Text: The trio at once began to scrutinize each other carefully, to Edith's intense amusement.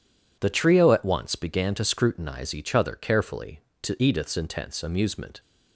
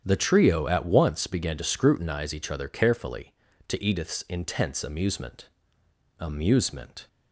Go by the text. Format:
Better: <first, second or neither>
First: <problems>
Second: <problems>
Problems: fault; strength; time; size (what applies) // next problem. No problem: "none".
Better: first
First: none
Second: starts louder than the rest; strong; until 1.0 s; 9 dB // says "amusement" twice; at 6.1 s